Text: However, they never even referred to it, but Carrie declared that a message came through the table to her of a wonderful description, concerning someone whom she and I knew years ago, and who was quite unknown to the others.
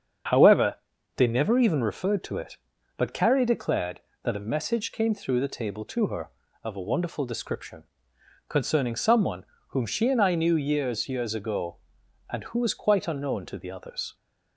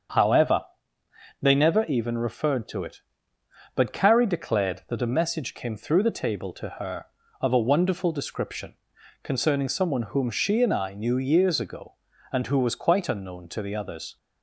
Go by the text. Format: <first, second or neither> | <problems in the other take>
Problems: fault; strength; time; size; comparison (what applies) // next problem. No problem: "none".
second | starts louder than the rest; strong; until 1.7 s; 7.5 dB; also in the second // pauses between "someone" and "whom"; slight; at 9.4 s; 0.24 s long // says "years" twice; at 11.0 s